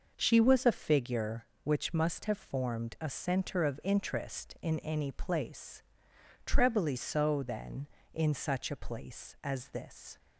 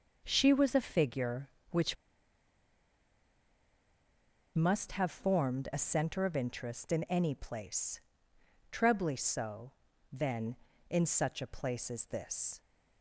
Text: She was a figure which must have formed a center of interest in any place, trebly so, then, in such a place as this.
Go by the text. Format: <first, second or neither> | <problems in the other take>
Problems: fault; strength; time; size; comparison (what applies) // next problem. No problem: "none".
first | pauses between "which" and "must"; strong; at 1.9 s; 2.6 s long